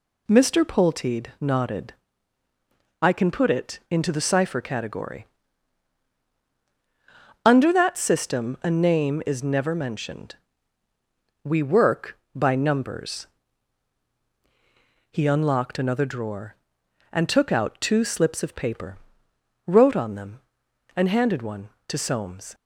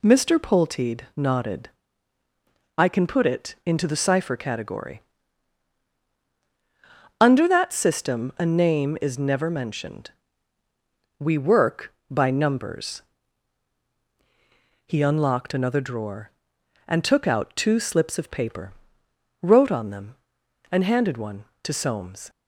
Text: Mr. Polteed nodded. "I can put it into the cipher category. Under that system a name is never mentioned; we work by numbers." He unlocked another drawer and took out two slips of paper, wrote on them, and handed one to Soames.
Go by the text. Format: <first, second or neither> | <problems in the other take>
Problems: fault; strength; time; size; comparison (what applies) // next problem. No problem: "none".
neither | none